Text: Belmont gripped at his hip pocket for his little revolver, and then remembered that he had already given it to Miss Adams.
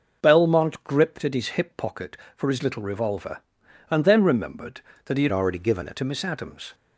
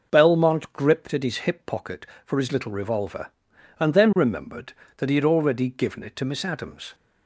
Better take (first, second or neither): second